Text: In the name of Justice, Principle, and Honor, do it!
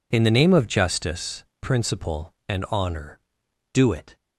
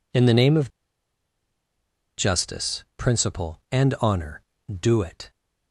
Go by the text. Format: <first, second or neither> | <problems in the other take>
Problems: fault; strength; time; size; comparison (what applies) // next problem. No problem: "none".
first | pauses between "of" and "Justice"; strong; at 0.6 s; 1.4 s long